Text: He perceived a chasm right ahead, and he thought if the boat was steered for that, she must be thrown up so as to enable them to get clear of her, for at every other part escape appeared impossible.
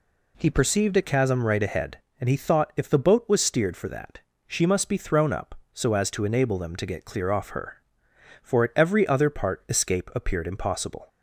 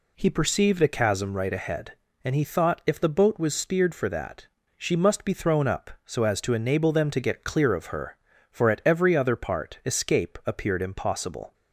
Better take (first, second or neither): second